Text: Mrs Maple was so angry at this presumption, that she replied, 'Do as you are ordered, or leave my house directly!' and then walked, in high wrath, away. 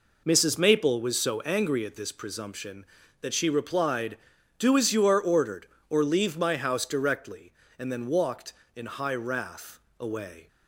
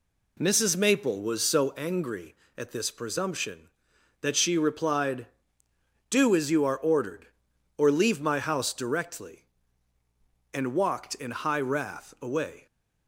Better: first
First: none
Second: skips "then"; at 10.7 s

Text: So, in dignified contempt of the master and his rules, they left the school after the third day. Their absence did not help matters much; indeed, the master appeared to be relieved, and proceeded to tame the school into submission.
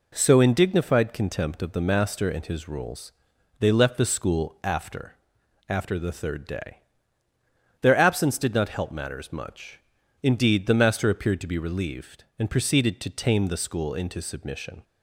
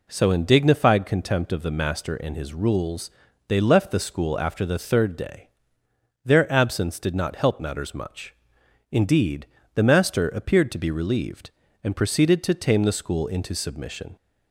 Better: second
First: says "after" twice; at 5.6 s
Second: none

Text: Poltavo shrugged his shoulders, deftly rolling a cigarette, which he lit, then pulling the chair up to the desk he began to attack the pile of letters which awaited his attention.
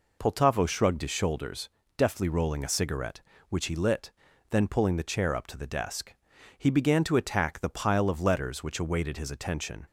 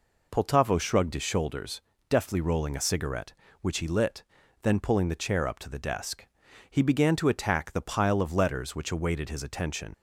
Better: first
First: pauses between "desk" and "he"; at 6.1 s; 0.44 s long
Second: pauses between "desk" and "he"; at 6.2 s; 0.44 s long // leaves "attention" unfinished; at 9.9 s; 35 ms

